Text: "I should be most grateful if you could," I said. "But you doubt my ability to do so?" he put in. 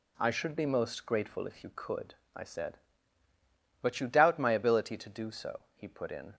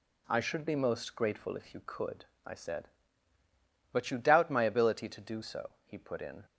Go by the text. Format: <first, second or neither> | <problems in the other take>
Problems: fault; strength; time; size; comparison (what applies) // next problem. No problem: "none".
neither | none